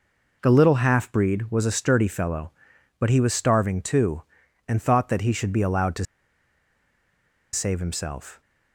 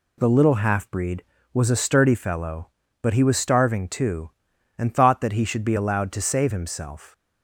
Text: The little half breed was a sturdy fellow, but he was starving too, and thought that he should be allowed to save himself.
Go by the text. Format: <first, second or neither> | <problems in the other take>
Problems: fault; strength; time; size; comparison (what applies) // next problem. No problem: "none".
second | pauses between "to" and "save"; strong; at 6.0 s; 1.4 s long